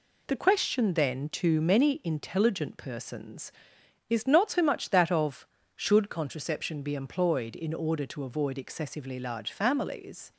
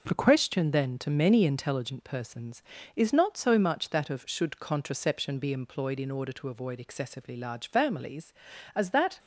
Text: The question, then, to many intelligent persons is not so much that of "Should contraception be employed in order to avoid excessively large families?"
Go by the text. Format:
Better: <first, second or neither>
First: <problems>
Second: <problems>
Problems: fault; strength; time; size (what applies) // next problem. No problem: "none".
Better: first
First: none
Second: goes on to say "as that"; slight; from 8.7 s on; 0.42 s long